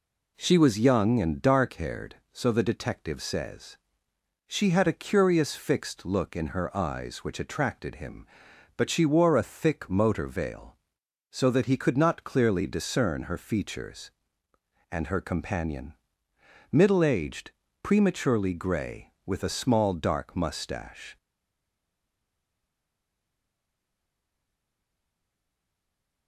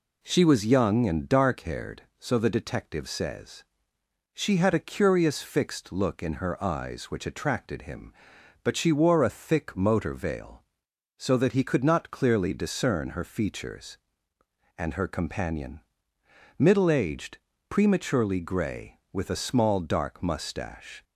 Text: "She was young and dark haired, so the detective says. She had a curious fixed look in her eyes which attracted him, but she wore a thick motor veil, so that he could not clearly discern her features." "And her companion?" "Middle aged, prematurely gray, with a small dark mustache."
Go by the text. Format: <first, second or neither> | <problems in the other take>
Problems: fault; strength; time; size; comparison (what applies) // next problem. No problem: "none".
second | stays silent after the last word; strong; from 21.1 s on; 5.1 s long